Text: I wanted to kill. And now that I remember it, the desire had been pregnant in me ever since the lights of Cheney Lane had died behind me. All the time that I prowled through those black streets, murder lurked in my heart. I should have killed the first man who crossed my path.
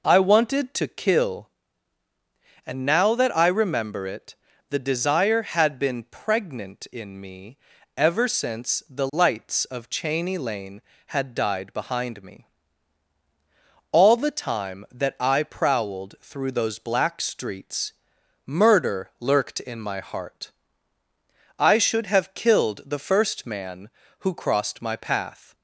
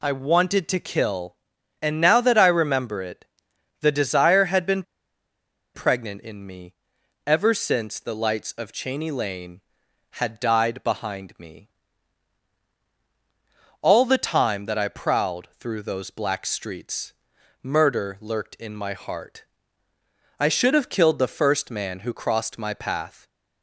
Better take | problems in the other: first | pauses between "been" and "pregnant"; noticeable; at 4.8 s; 0.92 s long // pauses between "me" and "ever"; noticeable; at 6.7 s; 0.52 s long; also in the first

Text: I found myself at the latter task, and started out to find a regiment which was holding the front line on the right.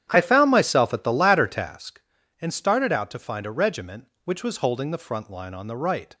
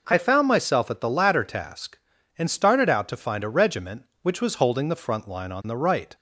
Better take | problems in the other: second | starts louder than the rest; strong; until 1.8 s; 10 dB

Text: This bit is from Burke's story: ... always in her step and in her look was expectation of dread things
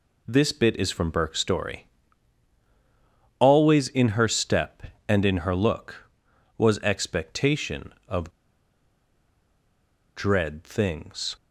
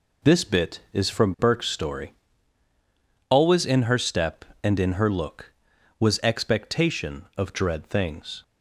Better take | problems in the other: second | pauses between "of" and "dread"; strong; at 8.3 s; 1.8 s long

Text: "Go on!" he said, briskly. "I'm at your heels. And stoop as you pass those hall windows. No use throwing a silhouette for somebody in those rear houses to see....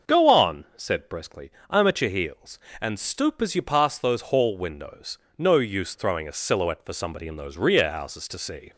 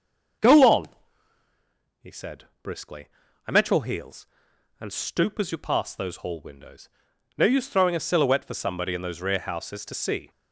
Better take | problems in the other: second | starts louder than the rest; until 1.2 s; 6.5 dB // skips "he"; at 0.7 s

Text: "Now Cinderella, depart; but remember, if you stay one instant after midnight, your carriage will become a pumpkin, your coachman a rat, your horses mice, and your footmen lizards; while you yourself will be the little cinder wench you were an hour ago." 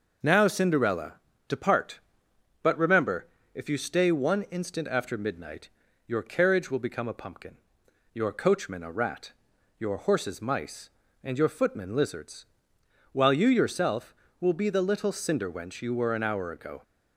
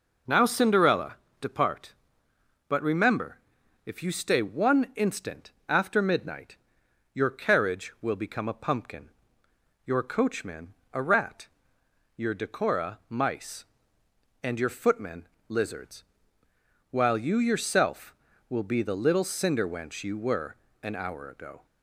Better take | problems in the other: first | pauses between "instant" and "after"; slight; at 5.5 s; 0.18 s long // pauses between "coachman" and "a"; slight; at 10.7 s; 0.20 s long // says "decora" for "horses"; at 12.3 s // pauses between "footmen" and "lizards"; slight; at 15.2 s; 0.20 s long // pauses between "were" and "an"; slight; at 20.5 s; 0.26 s long

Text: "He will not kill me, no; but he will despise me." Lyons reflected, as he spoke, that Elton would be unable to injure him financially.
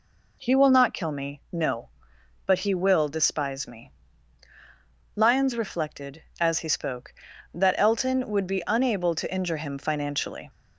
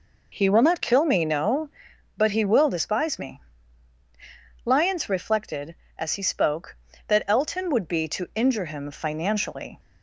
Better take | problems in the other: first | skips "unable"; at 8.0 s

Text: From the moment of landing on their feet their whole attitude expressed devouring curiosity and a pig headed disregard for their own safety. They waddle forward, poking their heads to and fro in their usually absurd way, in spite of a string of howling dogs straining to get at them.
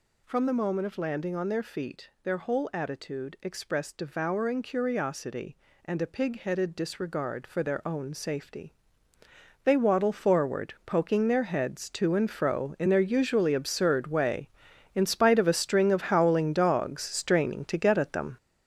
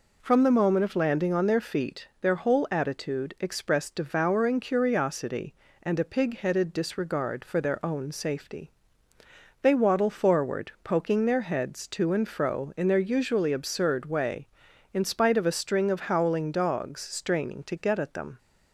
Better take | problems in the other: second | gets louder; strong; throughout; 8 dB

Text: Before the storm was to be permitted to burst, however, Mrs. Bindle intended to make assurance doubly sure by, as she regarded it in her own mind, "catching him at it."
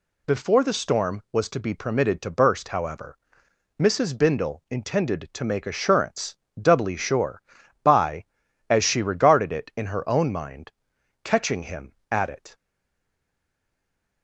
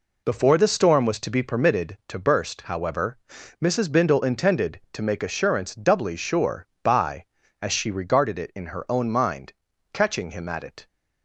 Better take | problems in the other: second | pauses between "assurance" and "doubly"; slight; at 6.3 s; 0.24 s long // stays silent after the last word; noticeable; from 12.5 s on; 1.7 s long

